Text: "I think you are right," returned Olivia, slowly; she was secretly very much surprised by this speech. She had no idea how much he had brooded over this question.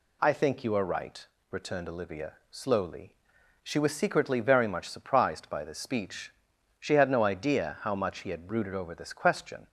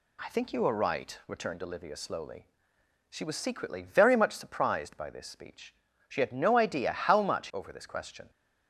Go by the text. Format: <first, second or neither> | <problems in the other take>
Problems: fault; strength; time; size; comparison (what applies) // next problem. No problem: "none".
first | skips "he had brooded"; at 7.4 s